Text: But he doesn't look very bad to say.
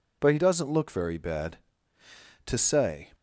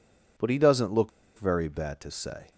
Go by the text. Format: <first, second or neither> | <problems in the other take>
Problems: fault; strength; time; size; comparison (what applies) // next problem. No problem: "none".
first | pauses between "look" and "very"; slight; at 1.0 s; 0.28 s long